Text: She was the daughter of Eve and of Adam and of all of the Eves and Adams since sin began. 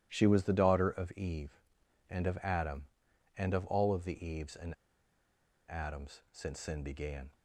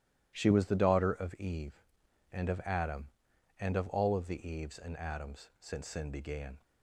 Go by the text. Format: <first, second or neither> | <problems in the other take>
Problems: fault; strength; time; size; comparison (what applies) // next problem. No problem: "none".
second | starts louder than the rest; strong; until 1.1 s; 13 dB; strong in the second // pauses between "and" and "Adams"; noticeable; at 4.7 s; 0.94 s long